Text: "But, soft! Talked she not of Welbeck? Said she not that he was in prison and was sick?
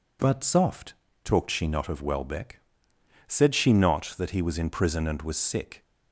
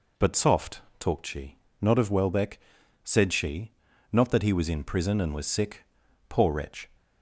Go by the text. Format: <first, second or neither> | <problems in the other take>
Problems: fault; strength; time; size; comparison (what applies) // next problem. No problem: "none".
first | pauses between "she" and "not"; slight; at 1.5 s; 0.24 s long // pauses between "she" and "not"; at 3.7 s; 0.40 s long // goes on to say "Poor wretch"; from 6.2 s on; 0.60 s long